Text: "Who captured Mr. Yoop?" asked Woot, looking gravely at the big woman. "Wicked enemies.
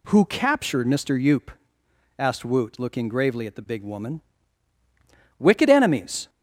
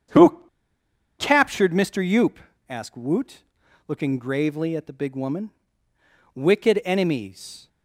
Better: first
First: none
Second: starts louder than the rest; strong; until 1.8 s; 8 dB // pauses between "Who" and "captured"; noticeable; at 0.4 s; 0.76 s long

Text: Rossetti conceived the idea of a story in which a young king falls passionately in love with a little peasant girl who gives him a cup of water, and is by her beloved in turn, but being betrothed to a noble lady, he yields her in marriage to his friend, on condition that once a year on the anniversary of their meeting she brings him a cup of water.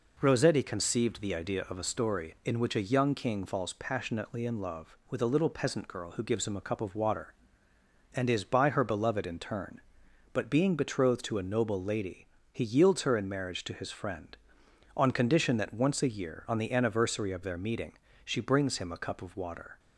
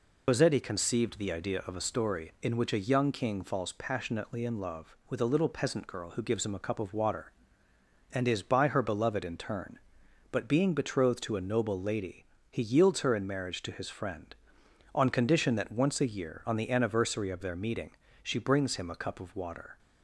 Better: first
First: pauses between "meeting" and "she"; slight; at 17.9 s; 0.32 s long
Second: loses the start of "Rossetti"; at 0.2 s; 120 ms // pauses between "meeting" and "she"; slight; at 17.9 s; 0.32 s long

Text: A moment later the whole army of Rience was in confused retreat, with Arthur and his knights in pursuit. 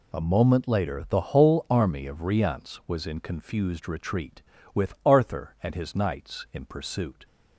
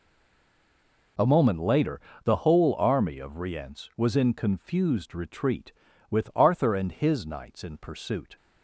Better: first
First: none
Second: stays silent before the first word; until 1.1 s; 1.1 s long // pauses between "later" and "the"; slight; at 2.0 s; 0.22 s long

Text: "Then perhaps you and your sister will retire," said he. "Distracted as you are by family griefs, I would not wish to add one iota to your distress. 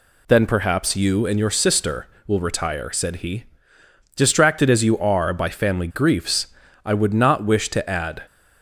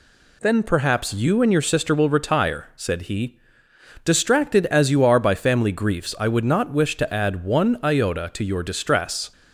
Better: second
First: stops before "one iota to your distress"; at 8.2 s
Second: none

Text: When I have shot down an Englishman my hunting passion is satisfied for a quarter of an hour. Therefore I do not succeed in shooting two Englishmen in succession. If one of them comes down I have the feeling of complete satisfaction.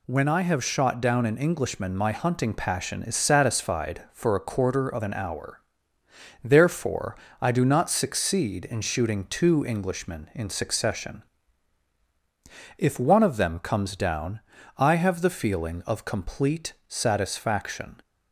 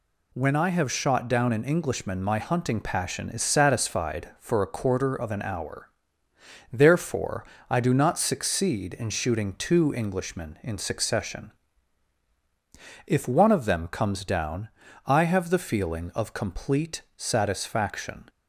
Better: neither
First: pauses between "Therefore" and "I"; slight; at 7.1 s; 0.24 s long // pauses between "down" and "I"; at 14.3 s; 0.38 s long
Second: pauses between "Therefore" and "I"; slight; at 7.4 s; 0.24 s long // pauses between "down" and "I"; at 14.6 s; 0.38 s long

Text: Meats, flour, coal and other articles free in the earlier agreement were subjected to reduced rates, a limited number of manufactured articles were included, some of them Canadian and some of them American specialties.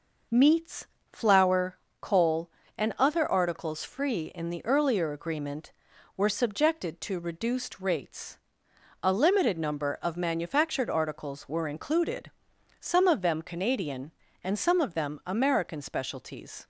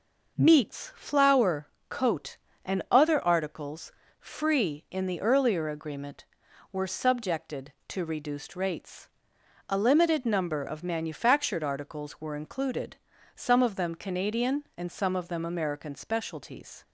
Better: first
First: none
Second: says "coat" for "coal"; at 1.8 s // pauses between "articles" and "free"; slight; at 3.9 s; 0.26 s long

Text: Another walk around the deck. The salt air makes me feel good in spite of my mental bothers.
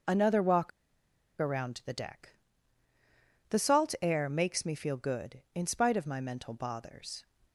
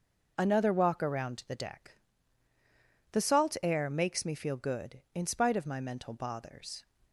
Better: second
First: pauses between "walk" and "around"; noticeable; at 0.7 s; 0.70 s long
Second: none

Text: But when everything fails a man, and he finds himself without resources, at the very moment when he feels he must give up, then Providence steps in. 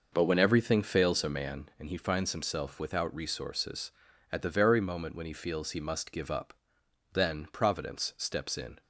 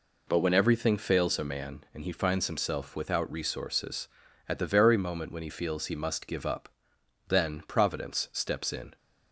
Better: second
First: starts louder than the rest; noticeable; until 1.8 s; 5.5 dB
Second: none

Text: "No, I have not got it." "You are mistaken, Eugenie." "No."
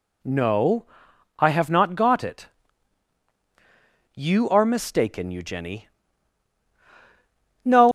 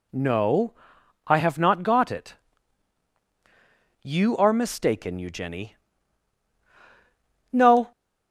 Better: second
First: leaves "No" unfinished; at 7.8 s; 120 ms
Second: none

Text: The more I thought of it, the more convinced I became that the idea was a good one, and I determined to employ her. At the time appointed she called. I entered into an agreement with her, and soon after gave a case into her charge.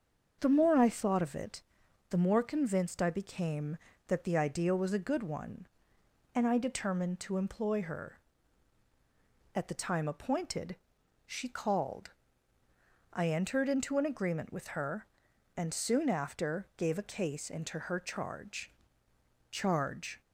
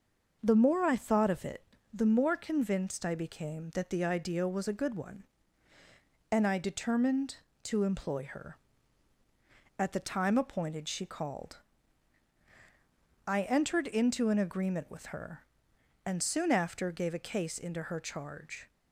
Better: second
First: starts louder than the rest; until 1.4 s; 7 dB // pauses between "appointed" and "she"; noticeable; at 10.7 s; 0.50 s long // says "charge" twice; at 19.5 s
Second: none

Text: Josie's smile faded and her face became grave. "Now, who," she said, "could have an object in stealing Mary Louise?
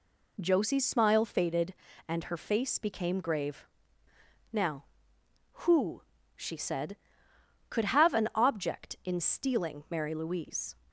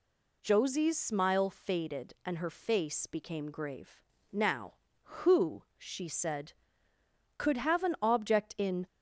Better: first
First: none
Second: stops before "stealing Mary Louise"; at 8.8 s

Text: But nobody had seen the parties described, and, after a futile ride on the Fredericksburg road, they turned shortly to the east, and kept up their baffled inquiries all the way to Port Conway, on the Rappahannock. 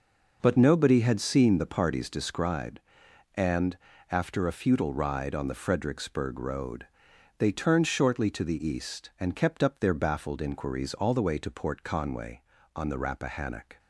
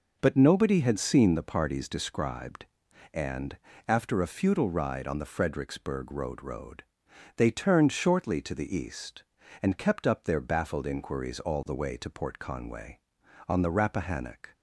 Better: first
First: none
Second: says "road" twice; at 6.4 s

